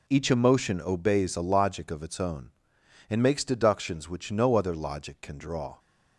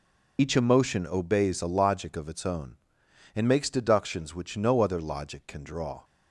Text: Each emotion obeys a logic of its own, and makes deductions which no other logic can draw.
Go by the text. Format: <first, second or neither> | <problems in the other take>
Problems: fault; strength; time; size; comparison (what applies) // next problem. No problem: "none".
first | loses the start of "Each"; at 0.3 s; 45 ms